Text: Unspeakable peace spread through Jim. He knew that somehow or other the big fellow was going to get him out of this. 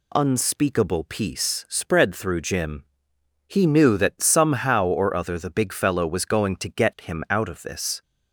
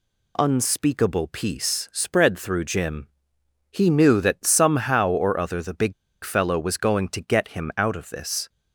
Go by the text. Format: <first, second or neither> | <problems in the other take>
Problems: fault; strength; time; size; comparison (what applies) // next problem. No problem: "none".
first | pauses between "big" and "fellow"; slight; at 5.9 s; 0.31 s long